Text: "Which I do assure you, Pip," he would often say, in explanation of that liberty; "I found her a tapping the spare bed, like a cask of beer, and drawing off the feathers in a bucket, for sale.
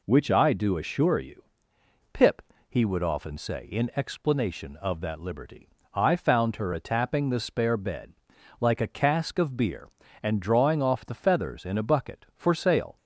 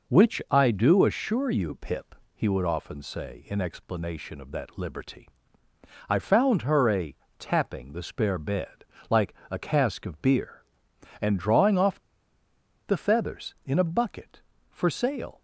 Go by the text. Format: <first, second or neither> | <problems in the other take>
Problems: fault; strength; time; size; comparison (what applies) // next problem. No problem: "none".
first | pauses between "a" and "tapping"; slight; at 7.1 s; 0.24 s long // pauses between "like" and "a"; slight; at 9.3 s; 0.16 s long // pauses between "off" and "the"; noticeable; at 11.9 s; 0.87 s long